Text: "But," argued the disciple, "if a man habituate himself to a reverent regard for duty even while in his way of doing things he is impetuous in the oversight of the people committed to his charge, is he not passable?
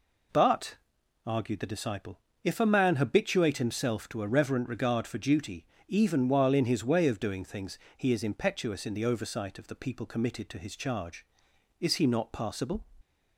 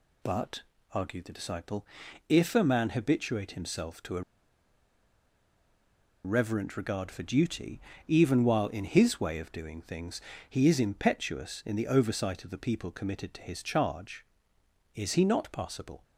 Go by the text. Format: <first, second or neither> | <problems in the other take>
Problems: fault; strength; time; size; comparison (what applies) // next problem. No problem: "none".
first | pauses between "a" and "reverent"; strong; at 4.2 s; 2.0 s long // pauses between "duty" and "even"; slight; at 7.7 s; 0.30 s long; slight in the first // pauses between "things" and "he"; slight; at 10.1 s; 0.30 s long; slight in the first